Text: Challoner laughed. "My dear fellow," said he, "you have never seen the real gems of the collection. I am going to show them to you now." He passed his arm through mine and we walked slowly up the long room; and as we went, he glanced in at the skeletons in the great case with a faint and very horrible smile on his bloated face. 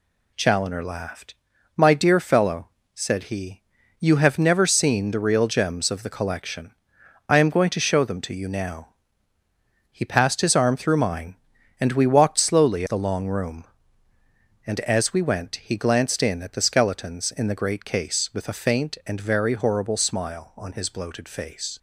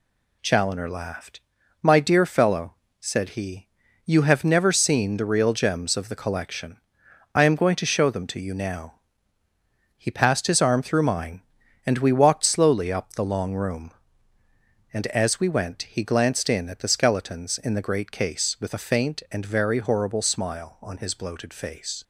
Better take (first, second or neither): second